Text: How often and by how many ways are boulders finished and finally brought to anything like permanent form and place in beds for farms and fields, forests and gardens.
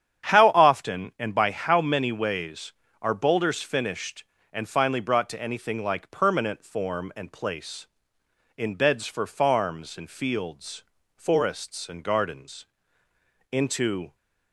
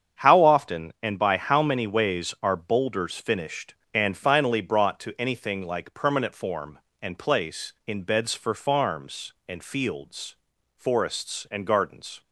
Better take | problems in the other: second | starts louder than the rest; strong; until 1.3 s; 9 dB; strong in the second // goes on to say "Into"; noticeable; from 13.5 s on; 0.62 s long

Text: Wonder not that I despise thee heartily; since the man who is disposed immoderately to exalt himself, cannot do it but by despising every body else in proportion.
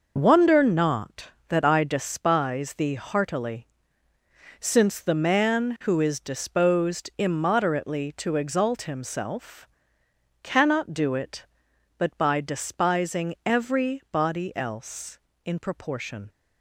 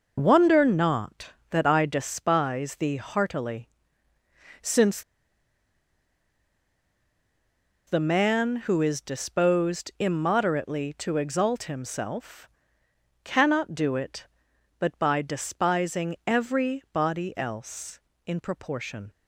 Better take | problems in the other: first | pauses between "since" and "the"; strong; at 5.0 s; 2.8 s long

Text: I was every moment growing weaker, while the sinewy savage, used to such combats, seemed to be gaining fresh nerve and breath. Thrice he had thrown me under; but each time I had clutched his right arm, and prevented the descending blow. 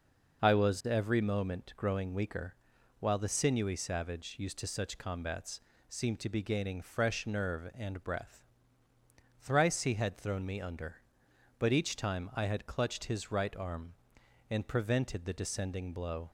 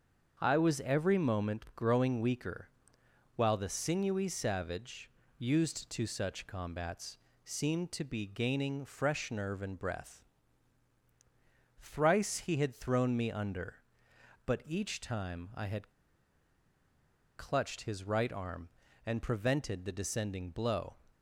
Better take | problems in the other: first | starts louder than the rest; until 1.4 s; 7 dB // pauses between "had" and "clutched"; strong; at 15.9 s; 1.4 s long

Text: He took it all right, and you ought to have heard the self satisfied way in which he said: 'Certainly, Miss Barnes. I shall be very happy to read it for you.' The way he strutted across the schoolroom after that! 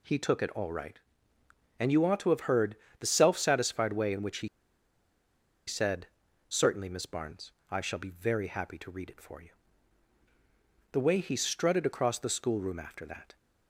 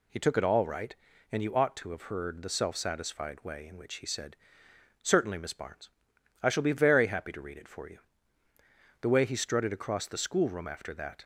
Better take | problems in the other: second | pauses between "heard" and "the"; slight; at 2.7 s; 0.24 s long // pauses between "he" and "said"; at 4.4 s; 1.1 s long

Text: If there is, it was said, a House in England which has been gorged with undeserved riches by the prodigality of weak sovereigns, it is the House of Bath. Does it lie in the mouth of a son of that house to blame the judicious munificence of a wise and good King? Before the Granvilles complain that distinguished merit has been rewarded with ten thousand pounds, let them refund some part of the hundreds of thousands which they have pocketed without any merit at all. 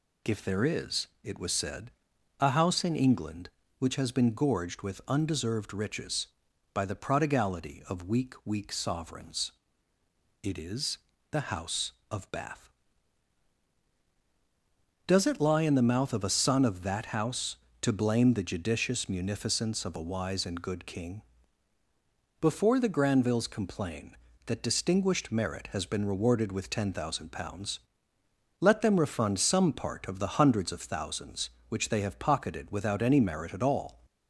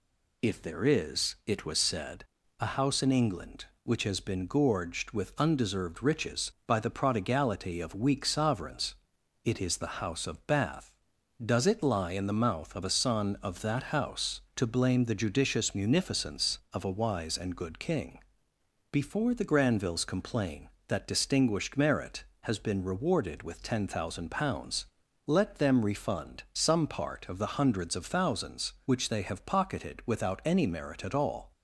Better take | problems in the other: second | says "weak" twice; at 8.4 s // pauses between "is" and "the"; slight; at 10.9 s; 0.32 s long

